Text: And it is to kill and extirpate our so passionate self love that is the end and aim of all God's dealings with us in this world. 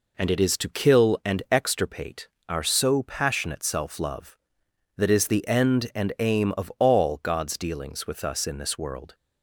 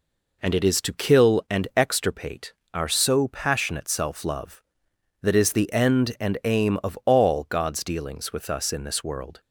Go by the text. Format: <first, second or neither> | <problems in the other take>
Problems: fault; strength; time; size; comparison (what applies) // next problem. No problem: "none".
neither | pauses between "extirpate" and "our"; slight; the same in both